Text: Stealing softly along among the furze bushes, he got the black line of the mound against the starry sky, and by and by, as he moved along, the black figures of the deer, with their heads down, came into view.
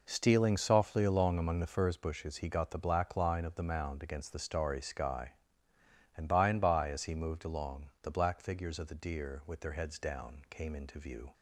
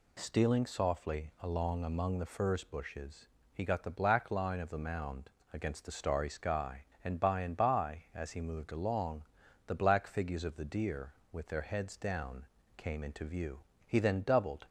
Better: first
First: none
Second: pauses between "mound" and "against"; slight; at 5.2 s; 0.24 s long // goes on to say "He then doubled"; noticeable; from 13.8 s on; 0.80 s long

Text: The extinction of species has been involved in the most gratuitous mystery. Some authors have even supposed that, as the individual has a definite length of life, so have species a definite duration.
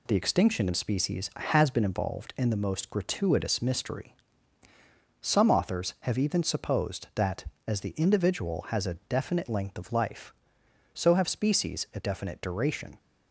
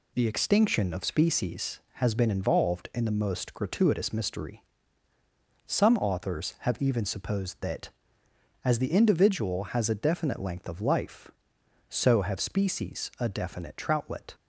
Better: first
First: none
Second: says "troutlet" for "duration"; at 13.7 s

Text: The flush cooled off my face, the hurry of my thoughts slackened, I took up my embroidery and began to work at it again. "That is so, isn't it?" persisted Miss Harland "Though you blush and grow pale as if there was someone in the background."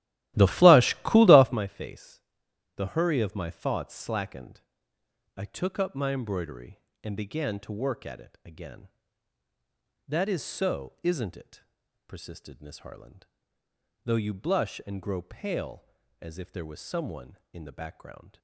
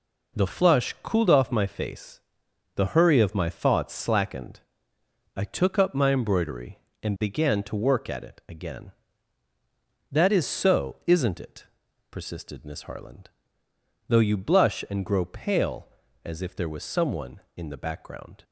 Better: second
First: starts louder than the rest; strong; until 1.6 s; 15.5 dB // pauses between "Harland" and "Though"; noticeable; at 13.2 s; 0.80 s long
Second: pauses between "Harland" and "Though"; noticeable; at 13.2 s; 0.80 s long

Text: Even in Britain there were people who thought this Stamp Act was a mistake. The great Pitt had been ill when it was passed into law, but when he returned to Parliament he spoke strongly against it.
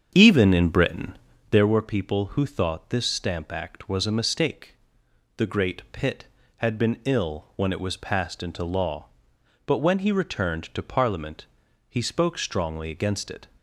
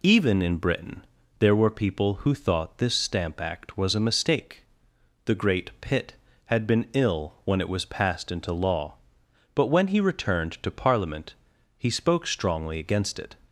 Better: second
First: starts louder than the rest; strong; until 1.7 s; 7.5 dB // pauses between "Britain" and "there"; slight; at 1.1 s; 0.36 s long // pauses between "Parliament" and "he"; noticeable; at 11.4 s; 0.46 s long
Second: pauses between "Britain" and "there"; slight; at 1.0 s; 0.36 s long // pauses between "Parliament" and "he"; noticeable; at 11.3 s; 0.46 s long

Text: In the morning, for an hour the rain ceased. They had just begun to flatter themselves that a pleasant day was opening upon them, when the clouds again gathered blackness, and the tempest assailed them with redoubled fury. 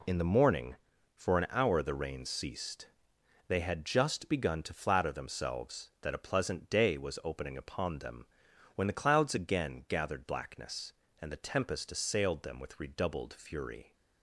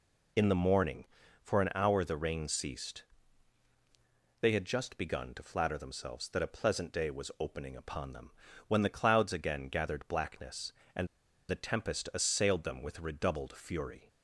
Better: first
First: none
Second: pauses between "and" and "the"; at 11.0 s; 0.42 s long

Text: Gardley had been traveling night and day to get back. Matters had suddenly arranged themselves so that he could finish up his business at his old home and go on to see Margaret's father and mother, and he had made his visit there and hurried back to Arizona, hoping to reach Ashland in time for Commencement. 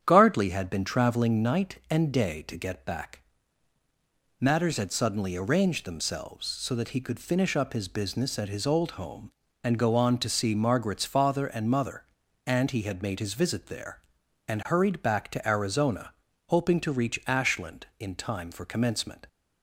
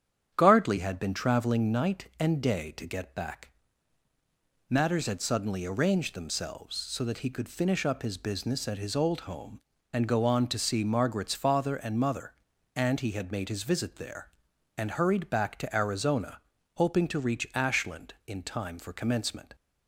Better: neither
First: starts louder than the rest; strong; until 1.0 s; 9 dB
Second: starts louder than the rest; strong; until 1.3 s; 9 dB

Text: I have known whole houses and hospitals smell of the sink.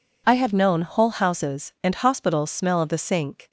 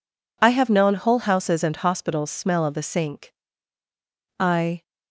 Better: first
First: none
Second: goes on to say "I"; slight; from 4.3 s on; 0.44 s long

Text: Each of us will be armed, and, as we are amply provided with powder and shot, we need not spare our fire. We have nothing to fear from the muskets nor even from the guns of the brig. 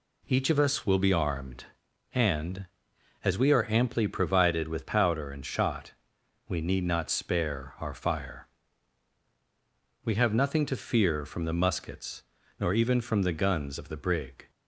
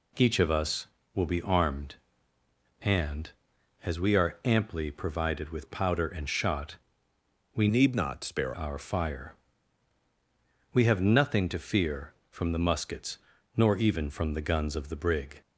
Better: first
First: pauses between "muskets" and "nor"; at 12.2 s; 0.38 s long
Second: changes voice from "need" to "spare"; from 7.6 to 8.5 s; 0.9 s long // pauses between "muskets" and "nor"; at 13.1 s; 0.42 s long

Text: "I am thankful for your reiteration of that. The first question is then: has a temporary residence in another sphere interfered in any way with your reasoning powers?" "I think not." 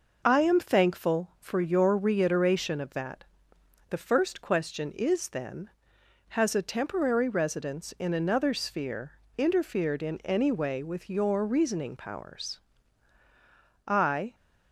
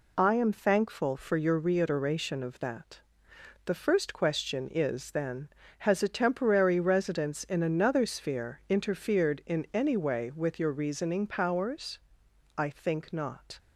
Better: second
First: pauses between "sphere" and "interfered"; slight; at 9.1 s; 0.18 s long // stops before "think not"; at 14.3 s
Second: none

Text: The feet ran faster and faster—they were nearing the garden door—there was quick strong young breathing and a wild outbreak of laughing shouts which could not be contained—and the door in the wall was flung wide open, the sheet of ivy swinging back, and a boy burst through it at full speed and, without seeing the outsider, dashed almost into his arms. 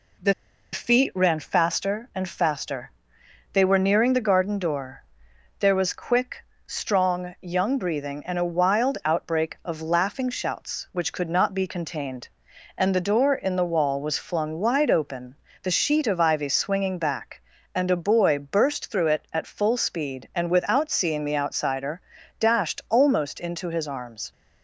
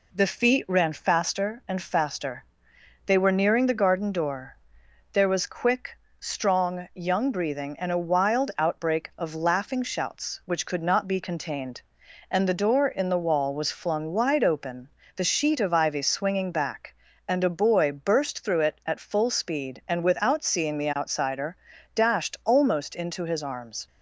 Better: second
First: pauses between "The" and "feet"; at 0.3 s; 0.39 s long // pauses between "quick" and "strong"; slight; at 6.4 s; 0.22 s long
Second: pauses between "quick" and "strong"; slight; at 5.9 s; 0.22 s long

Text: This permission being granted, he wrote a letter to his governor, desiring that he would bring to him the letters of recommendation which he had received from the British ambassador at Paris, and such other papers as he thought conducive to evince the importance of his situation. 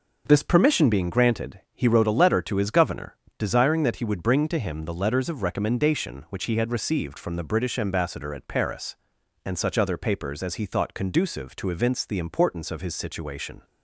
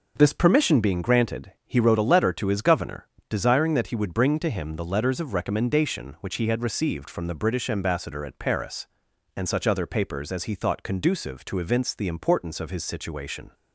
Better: neither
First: none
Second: none

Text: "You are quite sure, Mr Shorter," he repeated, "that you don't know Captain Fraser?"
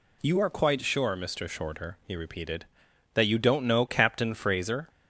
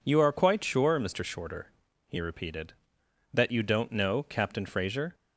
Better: neither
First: none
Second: none

